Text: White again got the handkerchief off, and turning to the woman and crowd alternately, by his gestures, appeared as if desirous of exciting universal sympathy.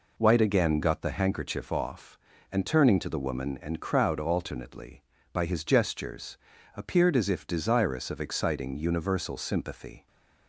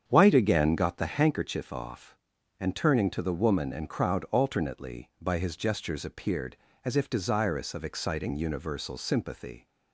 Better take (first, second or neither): first